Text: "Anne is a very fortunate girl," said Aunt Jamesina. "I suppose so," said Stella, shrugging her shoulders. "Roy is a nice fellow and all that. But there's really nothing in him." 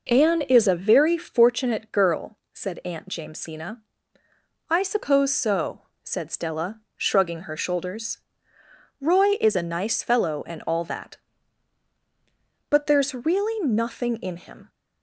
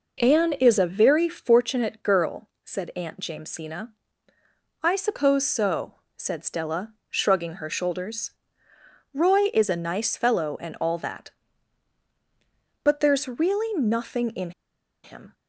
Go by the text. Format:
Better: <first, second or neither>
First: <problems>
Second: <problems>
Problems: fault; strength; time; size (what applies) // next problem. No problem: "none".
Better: first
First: none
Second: pauses between "in" and "him"; noticeable; at 14.5 s; 0.53 s long